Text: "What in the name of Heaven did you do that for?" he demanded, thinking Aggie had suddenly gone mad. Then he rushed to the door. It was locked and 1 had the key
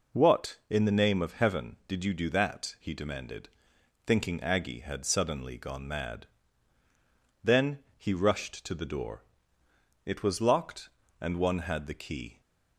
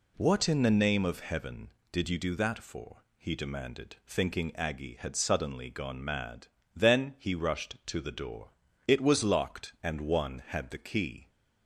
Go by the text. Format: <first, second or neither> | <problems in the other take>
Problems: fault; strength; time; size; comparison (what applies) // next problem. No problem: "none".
second | skips "for"; at 2.7 s